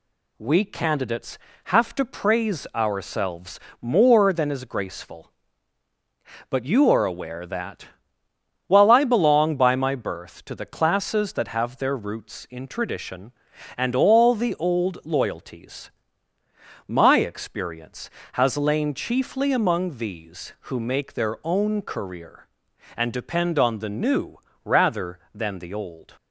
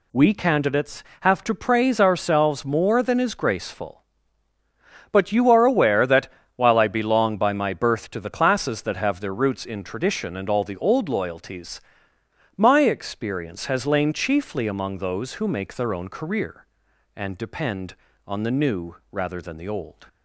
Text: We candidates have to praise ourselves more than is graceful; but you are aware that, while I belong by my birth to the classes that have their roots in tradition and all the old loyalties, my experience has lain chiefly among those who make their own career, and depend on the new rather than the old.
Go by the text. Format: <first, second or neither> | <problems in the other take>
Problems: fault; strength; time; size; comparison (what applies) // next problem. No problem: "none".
second | pauses between "ourselves" and "more"; slight; at 3.5 s; 0.22 s long // says "these" for "those"; at 19.9 s // pauses between "new" and "rather"; slight; at 24.3 s; 0.30 s long; slight in the second